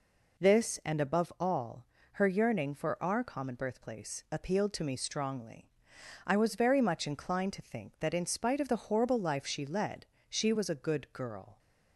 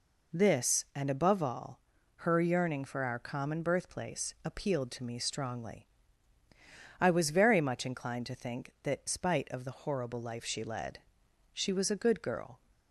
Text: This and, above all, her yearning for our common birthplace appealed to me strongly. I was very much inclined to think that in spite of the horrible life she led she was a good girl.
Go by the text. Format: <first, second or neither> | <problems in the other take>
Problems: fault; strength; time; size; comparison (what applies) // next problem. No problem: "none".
first | skips "in"; at 9.0 s // pauses between "led" and "she"; noticeable; at 10.9 s; 0.54 s long; slight in the first